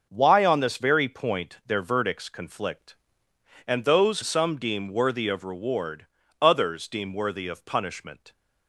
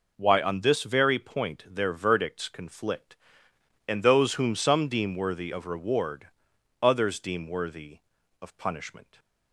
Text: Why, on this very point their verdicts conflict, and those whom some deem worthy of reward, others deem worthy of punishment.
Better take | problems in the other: second | skips "whom"; at 4.2 s

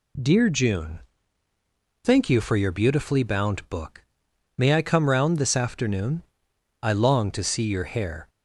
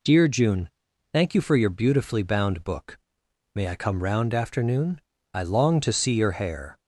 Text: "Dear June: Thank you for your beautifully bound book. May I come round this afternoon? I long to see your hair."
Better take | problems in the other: first | skips "this"; at 4.3 s

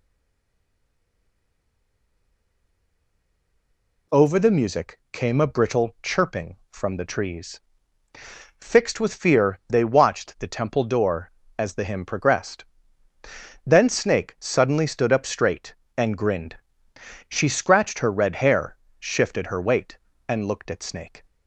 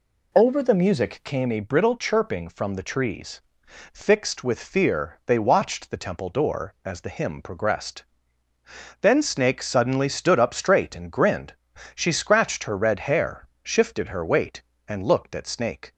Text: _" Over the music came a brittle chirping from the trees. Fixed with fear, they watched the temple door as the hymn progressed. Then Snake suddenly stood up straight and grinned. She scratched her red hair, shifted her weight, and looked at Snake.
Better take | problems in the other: second | stays silent before the first word; strong; until 4.0 s; 4.0 s long

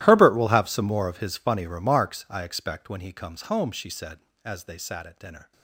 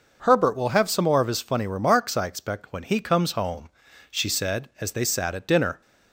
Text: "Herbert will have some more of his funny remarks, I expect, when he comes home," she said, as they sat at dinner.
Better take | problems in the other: second | gets quieter; strong; throughout; 20 dB

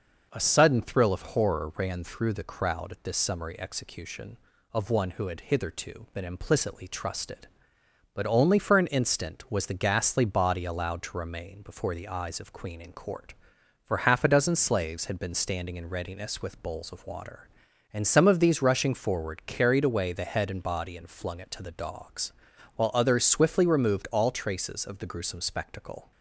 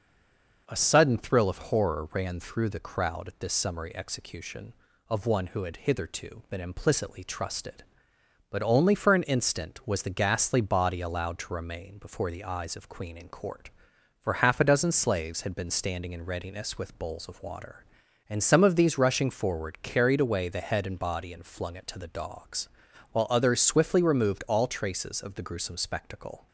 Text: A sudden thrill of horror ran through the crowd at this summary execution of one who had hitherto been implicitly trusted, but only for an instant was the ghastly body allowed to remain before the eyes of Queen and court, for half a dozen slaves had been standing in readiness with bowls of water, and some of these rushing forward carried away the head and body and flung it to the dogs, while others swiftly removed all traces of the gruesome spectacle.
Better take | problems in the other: first | stays silent before the first word; slight; until 0.6 s; 0.6 s long

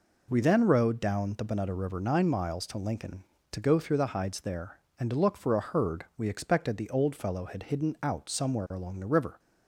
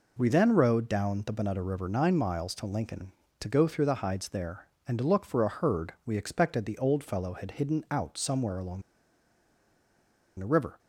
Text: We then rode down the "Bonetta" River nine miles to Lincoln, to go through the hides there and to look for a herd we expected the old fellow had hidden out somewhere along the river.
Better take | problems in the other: first | pauses between "along" and "the"; strong; at 8.8 s; 1.5 s long

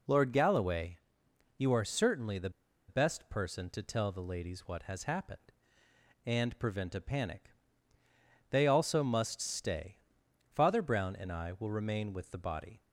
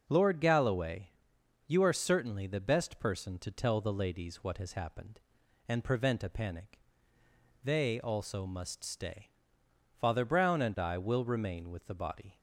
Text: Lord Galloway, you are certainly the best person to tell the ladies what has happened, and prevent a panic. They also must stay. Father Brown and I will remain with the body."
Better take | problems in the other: second | pauses between "the" and "best"; at 2.4 s; 0.38 s long

